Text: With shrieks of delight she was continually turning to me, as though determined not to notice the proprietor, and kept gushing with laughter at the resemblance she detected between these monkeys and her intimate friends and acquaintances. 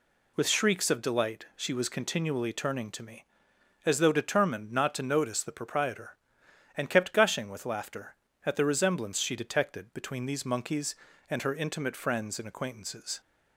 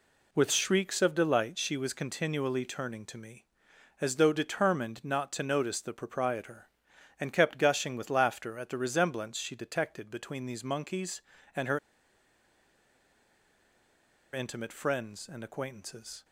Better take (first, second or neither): first